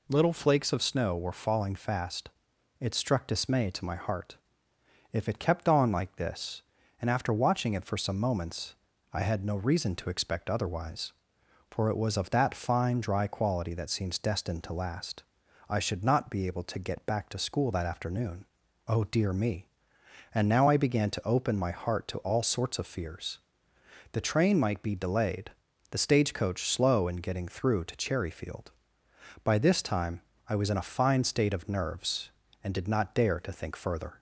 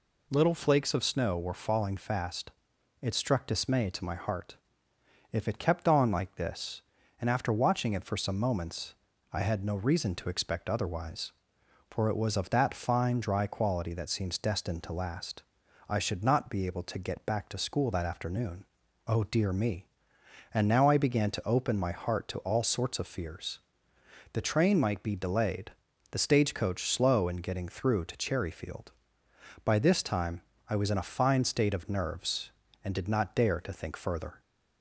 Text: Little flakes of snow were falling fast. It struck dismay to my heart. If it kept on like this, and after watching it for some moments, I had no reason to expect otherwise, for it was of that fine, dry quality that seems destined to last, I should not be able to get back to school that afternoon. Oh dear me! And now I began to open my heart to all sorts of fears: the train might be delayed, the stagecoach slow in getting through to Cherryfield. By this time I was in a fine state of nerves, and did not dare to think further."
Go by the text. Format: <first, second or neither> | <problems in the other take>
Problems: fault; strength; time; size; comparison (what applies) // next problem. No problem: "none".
neither | pauses between "time" and "I"; slight; the same in both